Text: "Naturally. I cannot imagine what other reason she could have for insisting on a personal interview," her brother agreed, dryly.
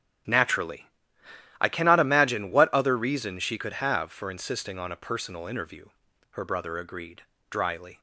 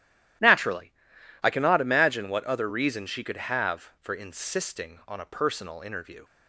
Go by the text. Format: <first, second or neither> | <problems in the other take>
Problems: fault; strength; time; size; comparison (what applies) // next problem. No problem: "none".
first | starts louder than the rest; strong; until 1.9 s; 13 dB; strong in the first // stops before "her brother agreed dryly"; at 6.2 s